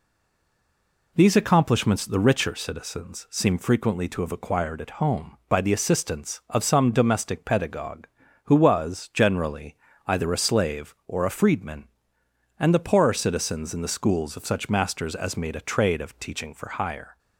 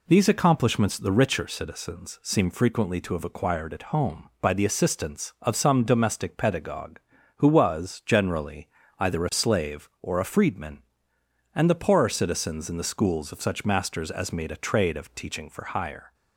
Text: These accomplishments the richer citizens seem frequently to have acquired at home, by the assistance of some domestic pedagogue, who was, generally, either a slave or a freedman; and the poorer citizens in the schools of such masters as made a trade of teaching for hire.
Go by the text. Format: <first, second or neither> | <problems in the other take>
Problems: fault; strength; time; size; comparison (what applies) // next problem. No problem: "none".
second | stays silent before the first word; until 1.1 s; 1.1 s long